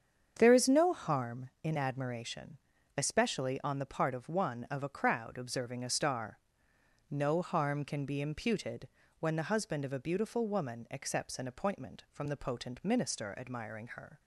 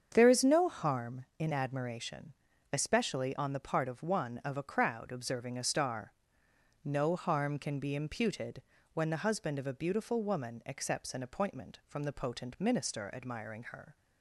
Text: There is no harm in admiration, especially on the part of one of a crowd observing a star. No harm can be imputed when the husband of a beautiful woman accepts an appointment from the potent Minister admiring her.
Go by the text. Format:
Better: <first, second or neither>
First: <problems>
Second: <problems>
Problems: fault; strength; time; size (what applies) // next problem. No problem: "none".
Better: neither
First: starts louder than the rest; strong; until 1.3 s; 7.5 dB // pauses between "imputed" and "when"; slight; at 8.8 s; 0.32 s long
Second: starts louder than the rest; strong; until 1.1 s; 7.5 dB // pauses between "imputed" and "when"; slight; at 8.6 s; 0.32 s long